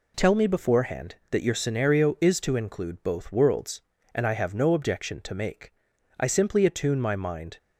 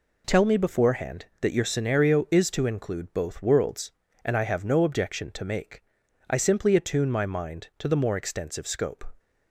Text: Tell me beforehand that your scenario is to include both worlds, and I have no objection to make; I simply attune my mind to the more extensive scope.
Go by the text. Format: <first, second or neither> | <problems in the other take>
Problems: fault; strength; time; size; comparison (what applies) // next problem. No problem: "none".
second | stops before "to the more extensive scope"; at 7.5 s